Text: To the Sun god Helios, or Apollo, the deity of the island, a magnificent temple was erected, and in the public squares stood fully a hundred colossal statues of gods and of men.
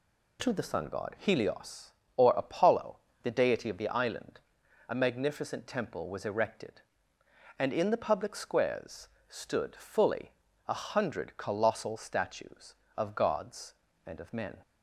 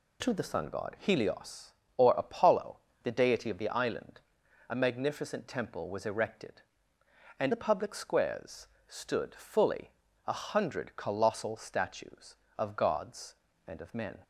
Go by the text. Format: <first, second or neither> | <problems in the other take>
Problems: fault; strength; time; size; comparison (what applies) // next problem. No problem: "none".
first | skips "in"; at 7.5 s // pauses between "squares" and "stood"; slight; at 8.6 s; 0.20 s long; slight in the first // pauses between "fully" and "a"; slight; at 9.8 s; 0.36 s long; slight in the first